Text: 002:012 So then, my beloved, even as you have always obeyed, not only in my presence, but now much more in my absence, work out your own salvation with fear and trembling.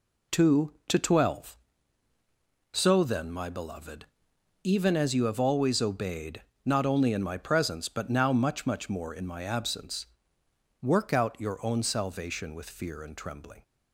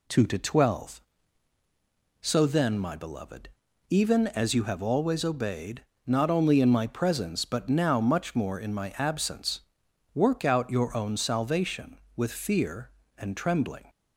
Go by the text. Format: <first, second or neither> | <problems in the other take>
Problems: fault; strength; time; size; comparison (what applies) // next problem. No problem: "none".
second | says "much" twice; at 8.6 s